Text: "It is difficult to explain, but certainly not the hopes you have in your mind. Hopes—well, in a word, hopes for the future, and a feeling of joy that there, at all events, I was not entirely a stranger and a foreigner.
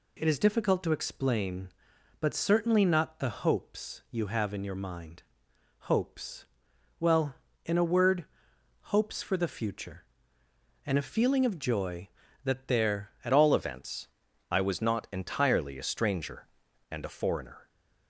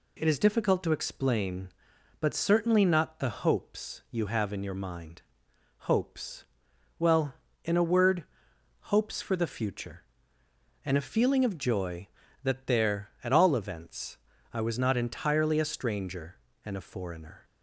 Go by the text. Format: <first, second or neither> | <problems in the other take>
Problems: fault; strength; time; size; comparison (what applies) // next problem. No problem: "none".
second | changes voice at "all"; from 13.3 s on; 4.3 s long